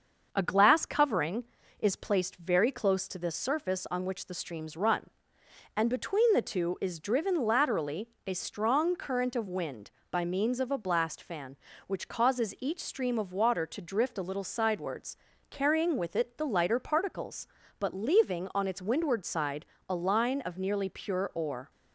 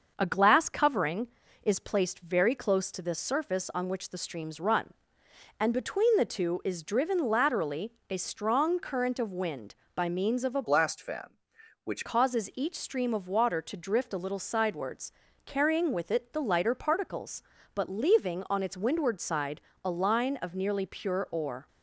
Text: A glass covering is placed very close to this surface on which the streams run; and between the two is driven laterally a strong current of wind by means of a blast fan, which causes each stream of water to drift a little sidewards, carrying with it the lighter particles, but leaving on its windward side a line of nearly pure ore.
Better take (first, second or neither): first